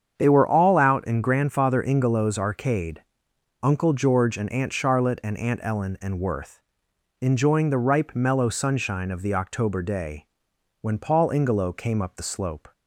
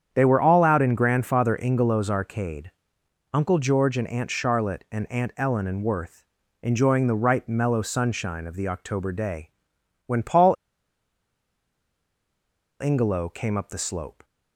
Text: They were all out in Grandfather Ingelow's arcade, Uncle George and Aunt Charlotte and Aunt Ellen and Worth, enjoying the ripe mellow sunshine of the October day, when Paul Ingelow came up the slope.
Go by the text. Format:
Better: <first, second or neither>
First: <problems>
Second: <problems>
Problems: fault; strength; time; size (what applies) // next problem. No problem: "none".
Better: first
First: starts louder than the rest; strong; until 1.1 s; 7.5 dB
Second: starts louder than the rest; strong; until 1.1 s; 8.5 dB // pauses between "Paul" and "Ingelow"; strong; at 10.5 s; 2.2 s long